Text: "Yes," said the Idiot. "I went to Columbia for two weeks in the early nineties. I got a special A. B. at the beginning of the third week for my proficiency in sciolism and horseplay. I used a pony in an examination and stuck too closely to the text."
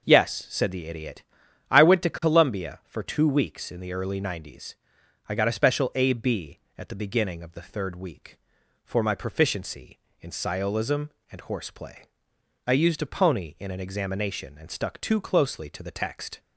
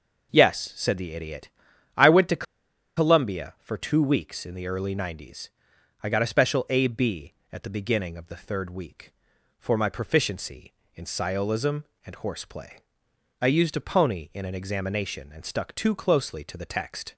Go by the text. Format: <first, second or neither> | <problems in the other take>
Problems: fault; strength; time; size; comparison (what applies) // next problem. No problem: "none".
first | pauses between "to" and "Columbia"; noticeable; at 2.4 s; 0.52 s long